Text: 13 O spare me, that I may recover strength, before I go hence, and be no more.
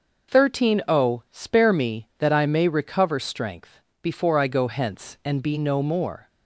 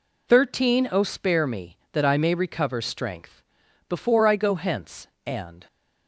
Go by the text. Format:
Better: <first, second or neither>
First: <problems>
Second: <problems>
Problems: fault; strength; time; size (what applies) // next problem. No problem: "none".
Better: first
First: none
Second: stops before "be no more"; at 5.6 s